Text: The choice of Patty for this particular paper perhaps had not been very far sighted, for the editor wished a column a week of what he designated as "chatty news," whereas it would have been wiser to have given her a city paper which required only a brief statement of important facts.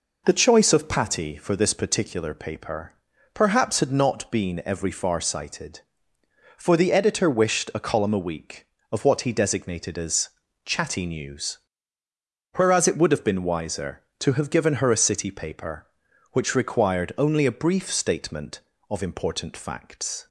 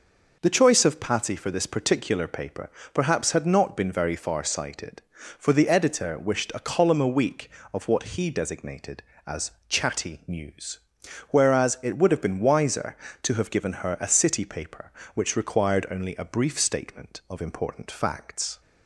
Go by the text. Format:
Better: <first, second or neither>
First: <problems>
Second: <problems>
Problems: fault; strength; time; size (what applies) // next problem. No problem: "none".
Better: second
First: pauses between "paper" and "perhaps"; at 2.9 s; 0.40 s long // says "every" for "very"; at 4.6 s // pauses between "as" and "chatty"; slight; at 10.2 s; 0.34 s long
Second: pauses between "paper" and "perhaps"; slight; at 2.7 s; 0.24 s long // pauses between "as" and "chatty"; slight; at 9.5 s; 0.18 s long